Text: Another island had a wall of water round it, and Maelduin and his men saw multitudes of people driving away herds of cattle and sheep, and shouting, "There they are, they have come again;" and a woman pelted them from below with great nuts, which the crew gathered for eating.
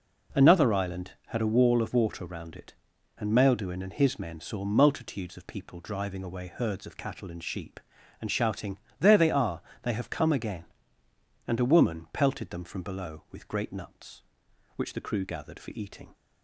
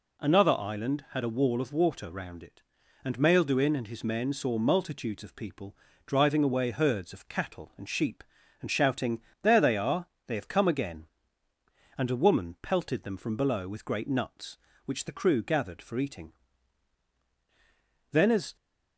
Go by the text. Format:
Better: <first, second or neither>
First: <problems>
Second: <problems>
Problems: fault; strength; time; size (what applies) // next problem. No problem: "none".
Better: first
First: none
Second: pauses between "people" and "driving"; slight; at 5.7 s; 0.30 s long // goes on to say "Then as"; slight; from 18.1 s on; 0.44 s long